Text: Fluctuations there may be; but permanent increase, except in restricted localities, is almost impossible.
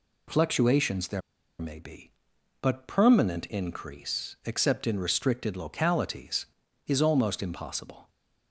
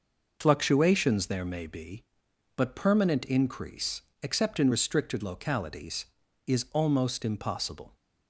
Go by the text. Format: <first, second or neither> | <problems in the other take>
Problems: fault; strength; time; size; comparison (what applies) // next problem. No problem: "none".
second | pauses between "there" and "may"; at 1.2 s; 0.40 s long